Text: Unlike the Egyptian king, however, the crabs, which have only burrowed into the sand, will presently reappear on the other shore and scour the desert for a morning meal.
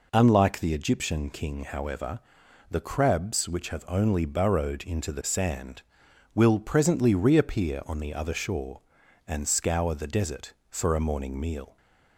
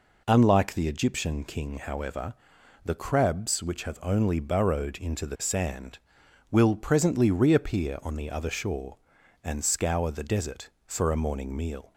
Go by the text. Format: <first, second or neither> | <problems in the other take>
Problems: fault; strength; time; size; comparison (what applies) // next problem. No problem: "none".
neither | none